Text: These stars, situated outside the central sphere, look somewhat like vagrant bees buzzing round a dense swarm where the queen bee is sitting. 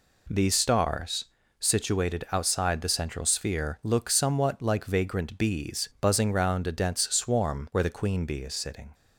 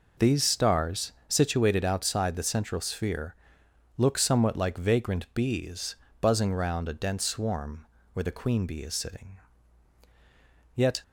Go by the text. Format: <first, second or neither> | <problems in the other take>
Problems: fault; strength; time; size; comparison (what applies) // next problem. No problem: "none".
first | pauses between "bees" and "buzzing"; slight; at 5.9 s; 0.26 s long // pauses between "swarm" and "where"; slight; at 7.8 s; 0.26 s long // goes on to say "Yet"; slight; from 10.7 s on; 0.28 s long